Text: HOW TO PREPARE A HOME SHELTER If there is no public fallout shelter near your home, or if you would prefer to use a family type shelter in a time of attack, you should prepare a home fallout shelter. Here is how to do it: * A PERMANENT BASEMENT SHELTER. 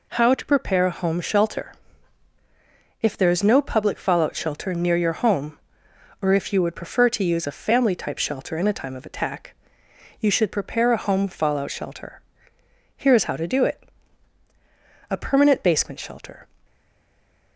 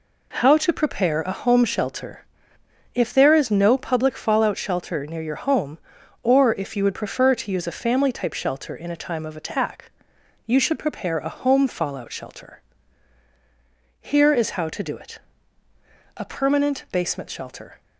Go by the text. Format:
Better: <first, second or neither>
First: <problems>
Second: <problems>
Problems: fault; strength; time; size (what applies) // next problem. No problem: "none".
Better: second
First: pauses between "SHELTER" and "If"; strong; at 1.7 s; 1.2 s long // stays silent after the last word; slight; from 16.6 s on; 0.9 s long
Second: pauses between "SHELTER" and "If"; noticeable; at 2.2 s; 0.70 s long